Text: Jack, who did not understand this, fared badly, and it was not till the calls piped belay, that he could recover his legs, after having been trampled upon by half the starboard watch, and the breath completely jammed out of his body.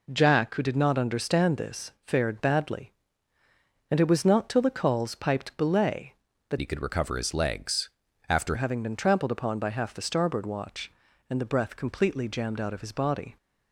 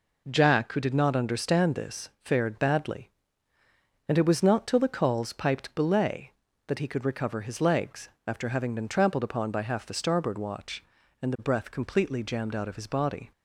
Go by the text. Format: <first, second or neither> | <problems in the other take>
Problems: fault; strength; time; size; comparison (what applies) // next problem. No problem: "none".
second | changes voice from "he" to "after"; from 6.6 to 8.5 s; 1.9 s long